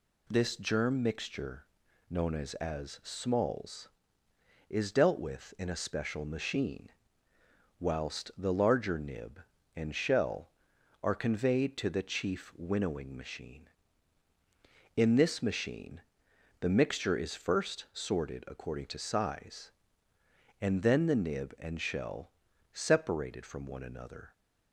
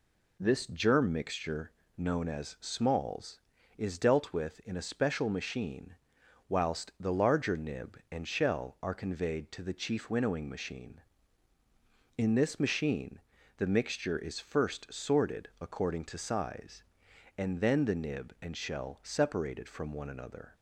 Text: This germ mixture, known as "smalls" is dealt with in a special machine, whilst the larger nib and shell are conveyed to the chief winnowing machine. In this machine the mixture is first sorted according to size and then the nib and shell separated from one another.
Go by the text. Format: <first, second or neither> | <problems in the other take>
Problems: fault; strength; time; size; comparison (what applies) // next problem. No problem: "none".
second | says "as" twice; at 2.5 s // pauses between "machine" and "the"; noticeable; at 16.0 s; 0.58 s long; also in the second // pauses between "shell" and "separated"; at 22.3 s; 0.42 s long